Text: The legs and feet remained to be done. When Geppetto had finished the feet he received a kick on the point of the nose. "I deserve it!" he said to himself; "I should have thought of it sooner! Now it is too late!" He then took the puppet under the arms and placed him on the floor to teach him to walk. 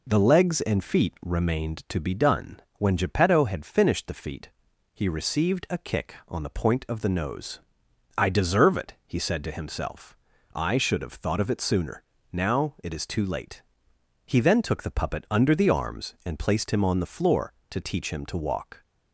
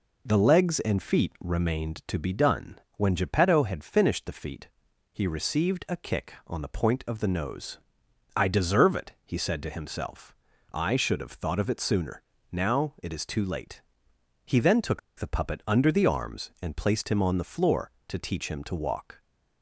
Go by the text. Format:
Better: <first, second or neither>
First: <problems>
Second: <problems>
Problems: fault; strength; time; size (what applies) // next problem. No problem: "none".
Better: first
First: pauses between "feet" and "he"; noticeable; at 4.4 s; 0.46 s long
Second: pauses between "feet" and "he"; noticeable; at 4.6 s; 0.46 s long // pauses between "took" and "the"; slight; at 14.9 s; 0.19 s long